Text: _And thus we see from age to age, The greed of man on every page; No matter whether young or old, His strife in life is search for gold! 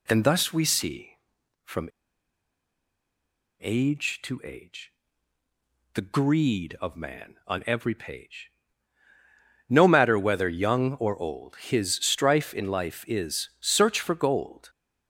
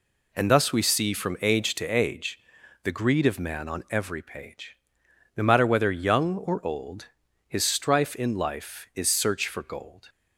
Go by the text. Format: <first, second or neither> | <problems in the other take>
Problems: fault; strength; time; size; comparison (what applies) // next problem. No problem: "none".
second | pauses between "from" and "age"; strong; at 1.8 s; 1.7 s long